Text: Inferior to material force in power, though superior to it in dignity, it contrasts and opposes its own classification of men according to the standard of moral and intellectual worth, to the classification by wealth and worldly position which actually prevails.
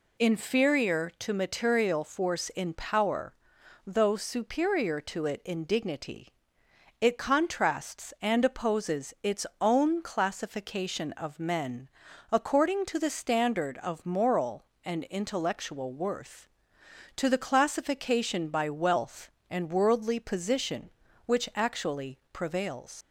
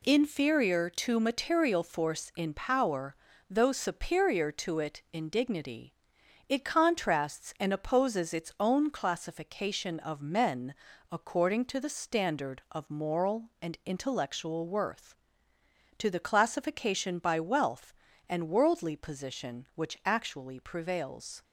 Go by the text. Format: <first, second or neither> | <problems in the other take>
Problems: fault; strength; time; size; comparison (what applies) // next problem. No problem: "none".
second | pauses between "its" and "own"; slight; at 9.4 s; 0.16 s long // pauses between "men" and "according"; at 11.8 s; 0.44 s long; slight in the second // pauses between "actually" and "prevails"; slight; at 22.1 s; 0.16 s long // leaves "prevails" unfinished; at 23.0 s; 105 ms